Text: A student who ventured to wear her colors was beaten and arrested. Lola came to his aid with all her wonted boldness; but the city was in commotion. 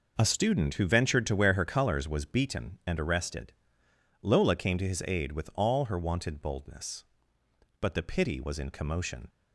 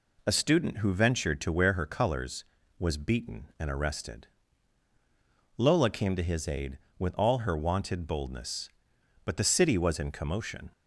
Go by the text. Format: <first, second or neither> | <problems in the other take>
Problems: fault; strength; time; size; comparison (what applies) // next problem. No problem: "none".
second | says "pity" for "city"; at 8.0 s